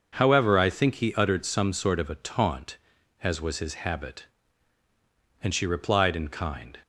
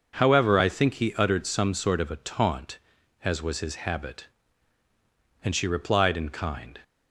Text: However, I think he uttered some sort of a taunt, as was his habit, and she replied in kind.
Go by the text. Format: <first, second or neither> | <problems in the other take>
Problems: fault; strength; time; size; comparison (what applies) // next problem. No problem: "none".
neither | none